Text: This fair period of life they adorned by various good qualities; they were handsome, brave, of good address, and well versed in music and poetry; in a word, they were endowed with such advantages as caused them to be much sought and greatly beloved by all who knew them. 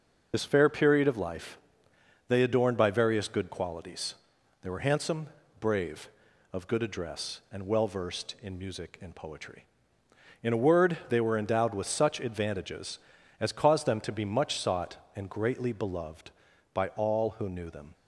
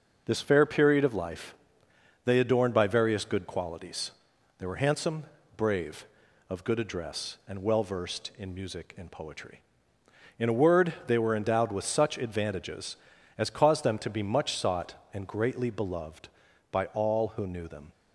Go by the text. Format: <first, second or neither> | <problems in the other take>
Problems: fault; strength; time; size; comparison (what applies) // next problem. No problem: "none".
second | loses the start of "This"; at 0.3 s; 45 ms // pauses between "life" and "they"; noticeable; at 1.5 s; 0.70 s long; noticeable in the second